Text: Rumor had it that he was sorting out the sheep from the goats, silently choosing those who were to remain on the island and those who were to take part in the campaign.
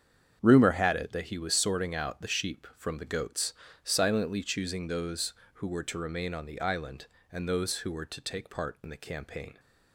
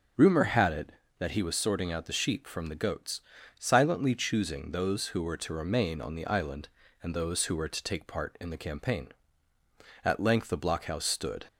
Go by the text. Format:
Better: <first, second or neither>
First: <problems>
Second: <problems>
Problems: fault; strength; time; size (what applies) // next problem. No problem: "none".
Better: first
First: starts louder than the rest; strong; until 1.4 s; 8 dB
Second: starts louder than the rest; until 1.4 s; 6.5 dB // goes on to say "At length the blockhouse stood"; from 10.0 s on; 1.4 s long